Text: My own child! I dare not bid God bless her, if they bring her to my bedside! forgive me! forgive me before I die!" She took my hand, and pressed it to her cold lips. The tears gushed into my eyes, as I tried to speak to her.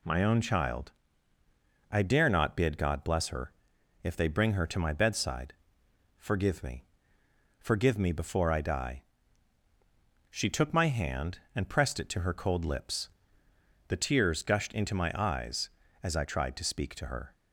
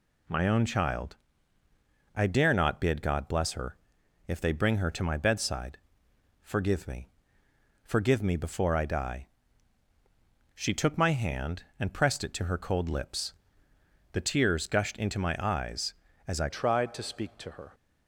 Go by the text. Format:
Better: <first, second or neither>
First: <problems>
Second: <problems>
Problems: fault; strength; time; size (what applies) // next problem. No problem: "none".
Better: first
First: none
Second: changes voice at "tried"; from 16.5 s on; 1.2 s long